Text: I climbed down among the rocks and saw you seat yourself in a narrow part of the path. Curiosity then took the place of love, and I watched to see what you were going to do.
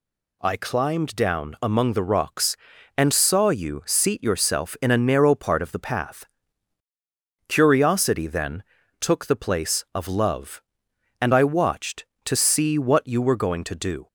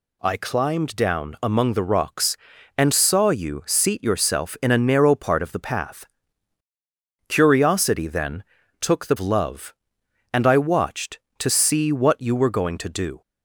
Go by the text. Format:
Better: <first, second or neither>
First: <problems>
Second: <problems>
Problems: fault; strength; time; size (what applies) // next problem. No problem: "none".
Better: first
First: pauses between "then" and "took"; at 8.6 s; 0.38 s long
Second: pauses between "then" and "took"; at 8.4 s; 0.38 s long // skips "place of"; at 9.1 s